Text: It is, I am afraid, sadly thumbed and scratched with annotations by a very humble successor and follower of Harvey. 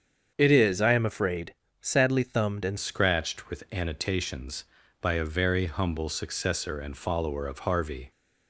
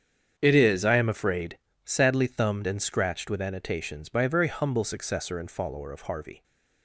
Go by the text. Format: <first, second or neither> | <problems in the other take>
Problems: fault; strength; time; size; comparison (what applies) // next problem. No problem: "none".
second | starts louder than the rest; strong; until 1.3 s; 7.5 dB; strong in the second // changes voice at "scratched"; from 2.7 s on; 5.4 s long